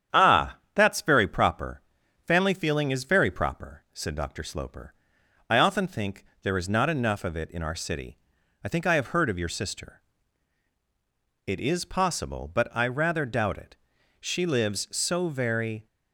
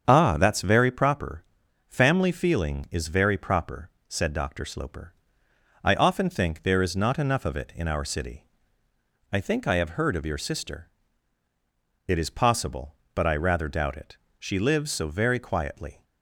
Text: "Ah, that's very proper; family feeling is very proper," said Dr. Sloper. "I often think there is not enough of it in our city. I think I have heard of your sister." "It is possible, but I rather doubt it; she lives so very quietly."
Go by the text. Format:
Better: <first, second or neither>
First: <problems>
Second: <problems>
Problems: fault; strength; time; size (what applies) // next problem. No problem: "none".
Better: second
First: starts louder than the rest; strong; until 1.2 s; 9 dB // pauses between "think" and "there"; slight; at 6.2 s; 0.18 s long // stops before "quietly"; at 15.8 s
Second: starts louder than the rest; strong; until 1.0 s; 7.5 dB